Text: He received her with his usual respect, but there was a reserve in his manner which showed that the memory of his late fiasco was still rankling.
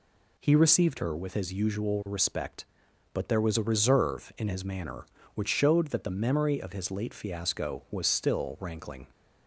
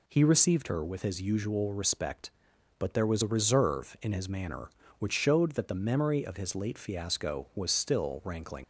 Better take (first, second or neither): first